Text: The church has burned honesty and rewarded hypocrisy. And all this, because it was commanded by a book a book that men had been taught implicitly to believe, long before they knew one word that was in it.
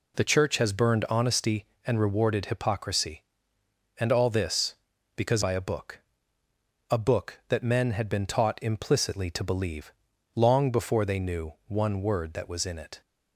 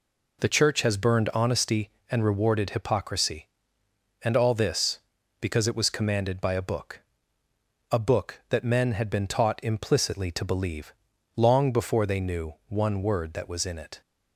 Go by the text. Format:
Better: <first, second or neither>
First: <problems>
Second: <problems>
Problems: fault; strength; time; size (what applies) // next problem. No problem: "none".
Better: second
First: skips "it was commanded"; at 5.4 s // pauses between "book" and "a"; noticeable; at 5.9 s; 0.92 s long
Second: pauses between "book" and "a"; noticeable; at 6.9 s; 0.92 s long